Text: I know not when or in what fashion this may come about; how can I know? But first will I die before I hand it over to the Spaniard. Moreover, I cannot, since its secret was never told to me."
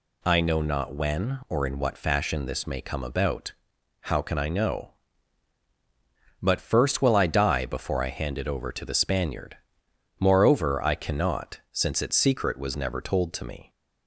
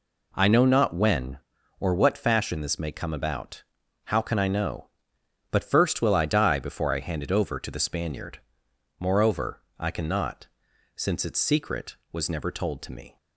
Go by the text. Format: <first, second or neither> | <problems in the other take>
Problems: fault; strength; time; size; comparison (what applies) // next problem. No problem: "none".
first | skips "in"; at 1.9 s